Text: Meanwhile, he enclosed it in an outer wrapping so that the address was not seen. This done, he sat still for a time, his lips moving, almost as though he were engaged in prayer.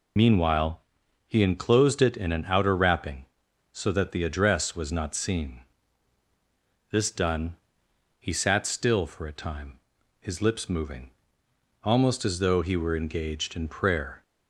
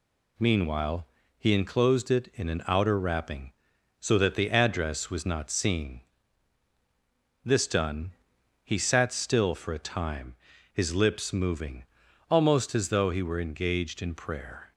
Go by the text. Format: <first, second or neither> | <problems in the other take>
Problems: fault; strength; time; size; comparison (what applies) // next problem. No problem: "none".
second | loses the start of "Meanwhile"; at 0.1 s; 50 ms